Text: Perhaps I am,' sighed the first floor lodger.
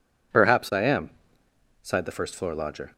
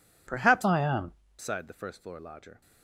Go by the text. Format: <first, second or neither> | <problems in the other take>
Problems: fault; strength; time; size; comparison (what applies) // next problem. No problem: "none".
first | changes voice from "I" to "am"; from 0.6 to 1.1 s; 0.5 s long